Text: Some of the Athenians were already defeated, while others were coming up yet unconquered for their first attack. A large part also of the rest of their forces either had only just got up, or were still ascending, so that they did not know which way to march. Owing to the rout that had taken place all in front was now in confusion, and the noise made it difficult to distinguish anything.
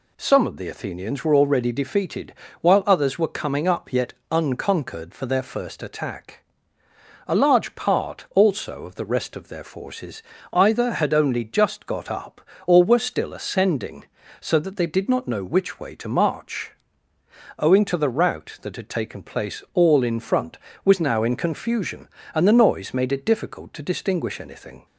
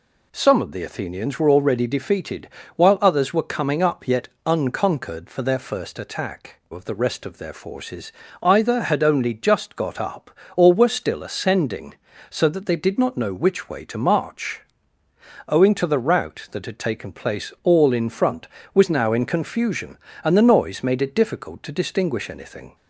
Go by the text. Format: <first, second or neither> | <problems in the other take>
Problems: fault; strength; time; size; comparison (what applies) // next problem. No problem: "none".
first | pauses between "yet" and "unconquered"; slight; at 4.2 s; 0.18 s long; slight in the first // skips "A large part also"; at 6.6 s // pauses between "forces" and "either"; slight; at 8.1 s; 0.30 s long; slight in the first